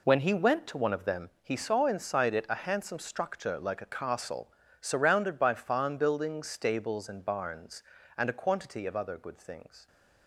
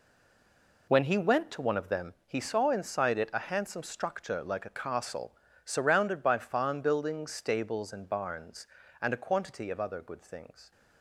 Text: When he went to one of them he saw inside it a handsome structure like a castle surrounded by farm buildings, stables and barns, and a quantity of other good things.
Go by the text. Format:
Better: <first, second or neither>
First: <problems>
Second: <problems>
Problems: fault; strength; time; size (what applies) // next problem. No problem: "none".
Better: first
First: pauses between "castle" and "surrounded"; slight; at 4.5 s; 0.28 s long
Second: stays silent before the first word; slight; until 0.8 s; 0.8 s long // pauses between "castle" and "surrounded"; slight; at 5.3 s; 0.28 s long